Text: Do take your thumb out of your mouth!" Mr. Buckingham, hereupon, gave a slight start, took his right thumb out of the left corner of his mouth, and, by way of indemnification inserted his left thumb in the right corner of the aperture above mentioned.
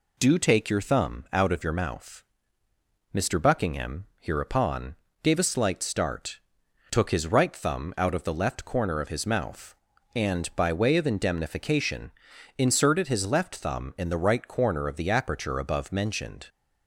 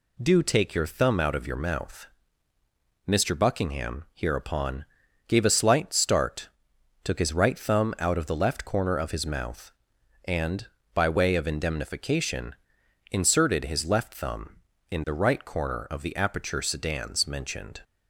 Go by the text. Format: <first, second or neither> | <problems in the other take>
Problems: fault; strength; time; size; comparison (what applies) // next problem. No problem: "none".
first | pauses between "indemnification" and "inserted"; noticeable; at 12.5 s; 0.54 s long; also in the first // says "sedans" for "above"; at 16.6 s